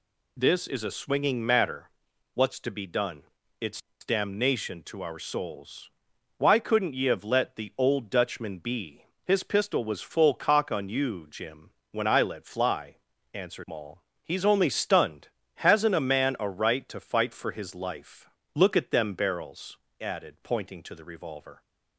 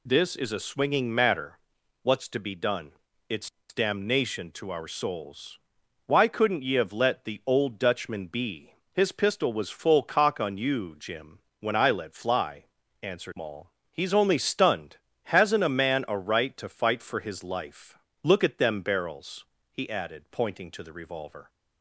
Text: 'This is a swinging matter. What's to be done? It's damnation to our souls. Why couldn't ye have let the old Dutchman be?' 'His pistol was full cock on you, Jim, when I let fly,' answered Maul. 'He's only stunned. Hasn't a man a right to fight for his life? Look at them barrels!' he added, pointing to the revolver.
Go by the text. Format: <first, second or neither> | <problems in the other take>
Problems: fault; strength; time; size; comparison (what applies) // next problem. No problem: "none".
second | pauses between "It's" and "damnation"; slight; at 3.8 s; 0.24 s long; slight in the second // skips "he"; at 19.8 s